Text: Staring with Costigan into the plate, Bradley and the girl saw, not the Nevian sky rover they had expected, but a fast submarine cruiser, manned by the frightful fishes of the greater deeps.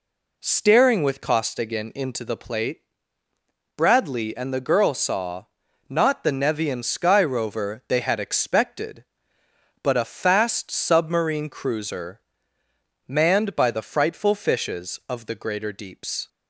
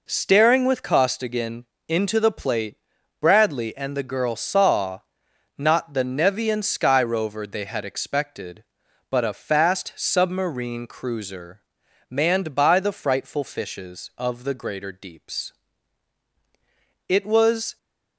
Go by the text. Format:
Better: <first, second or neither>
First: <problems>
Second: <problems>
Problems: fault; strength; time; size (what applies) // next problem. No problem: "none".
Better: first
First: none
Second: pauses between "Costigan" and "into"; slight; at 1.6 s; 0.24 s long // goes on to say "It was"; noticeable; from 17.0 s on; 0.68 s long